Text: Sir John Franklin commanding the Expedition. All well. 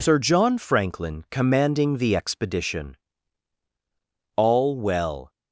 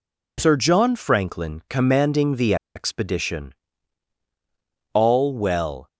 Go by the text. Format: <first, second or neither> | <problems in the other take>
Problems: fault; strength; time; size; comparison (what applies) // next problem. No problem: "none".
first | pauses between "the" and "Expedition"; slight; at 2.5 s; 0.20 s long